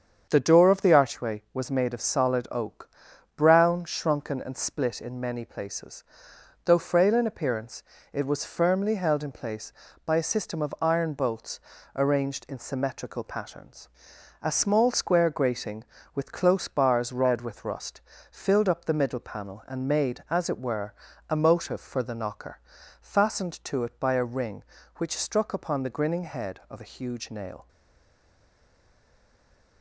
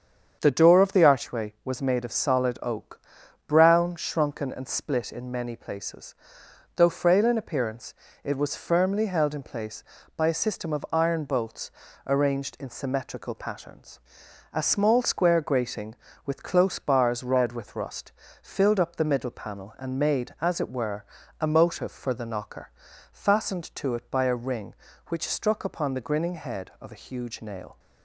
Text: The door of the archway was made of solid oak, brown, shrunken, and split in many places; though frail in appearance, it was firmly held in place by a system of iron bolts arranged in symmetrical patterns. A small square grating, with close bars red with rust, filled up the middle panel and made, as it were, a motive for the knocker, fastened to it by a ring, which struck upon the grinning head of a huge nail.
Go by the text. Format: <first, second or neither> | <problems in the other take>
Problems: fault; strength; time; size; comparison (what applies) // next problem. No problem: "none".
second | starts louder than the rest; strong; until 1.3 s; 7.5 dB; strong in the second // pauses between "bolts" and "arranged"; slight; at 11.5 s; 0.34 s long; slight in the second // stays silent after the last word; from 27.6 s on; 2.2 s long